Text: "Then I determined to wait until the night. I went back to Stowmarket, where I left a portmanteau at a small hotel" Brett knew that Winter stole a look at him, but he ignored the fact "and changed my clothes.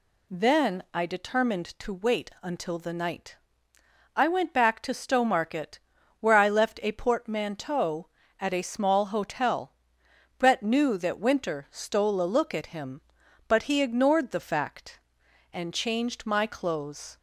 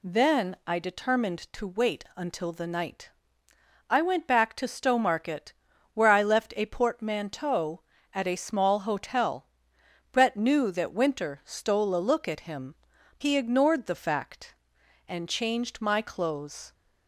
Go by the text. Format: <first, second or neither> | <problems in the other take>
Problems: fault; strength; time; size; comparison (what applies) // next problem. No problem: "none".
first | pauses between "hotel" and "Brett"; noticeable; at 9.4 s; 0.64 s long; noticeable in the first // skips "but"; at 12.9 s